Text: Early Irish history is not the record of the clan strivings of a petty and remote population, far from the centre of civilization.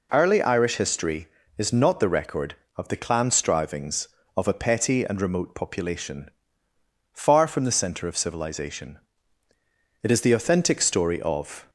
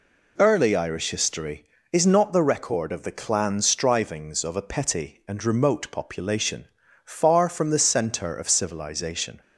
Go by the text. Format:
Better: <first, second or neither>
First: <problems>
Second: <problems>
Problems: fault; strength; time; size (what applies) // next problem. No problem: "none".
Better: second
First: goes on to say "It is the authentic story of"; strong; from 10.0 s on; 1.6 s long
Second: none